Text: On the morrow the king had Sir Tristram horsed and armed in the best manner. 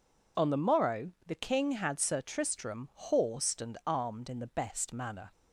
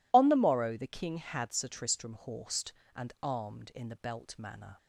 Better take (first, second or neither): first